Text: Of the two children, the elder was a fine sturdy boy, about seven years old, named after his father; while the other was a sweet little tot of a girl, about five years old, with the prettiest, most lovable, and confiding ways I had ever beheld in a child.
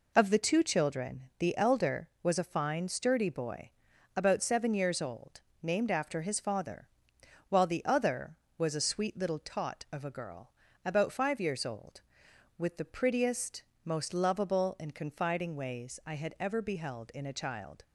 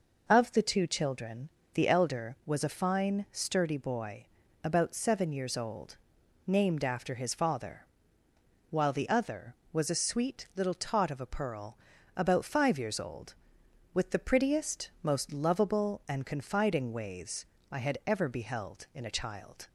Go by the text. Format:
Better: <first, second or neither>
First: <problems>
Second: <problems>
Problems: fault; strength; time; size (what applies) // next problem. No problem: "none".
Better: first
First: none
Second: says "pearl" for "girl"; at 11.2 s // pauses between "ways" and "I"; slight; at 17.4 s; 0.26 s long